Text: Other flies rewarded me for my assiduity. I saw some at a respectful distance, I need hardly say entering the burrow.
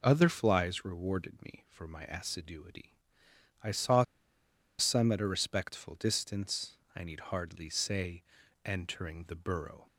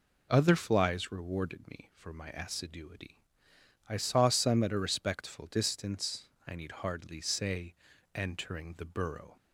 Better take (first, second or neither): second